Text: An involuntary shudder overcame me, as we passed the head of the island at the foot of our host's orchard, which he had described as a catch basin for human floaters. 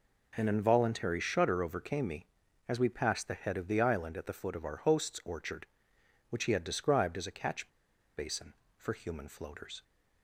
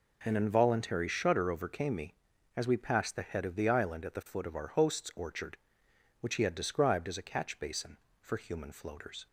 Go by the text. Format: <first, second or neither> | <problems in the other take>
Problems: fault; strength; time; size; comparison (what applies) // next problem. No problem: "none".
second | pauses between "catch" and "basin"; noticeable; at 7.6 s; 0.49 s long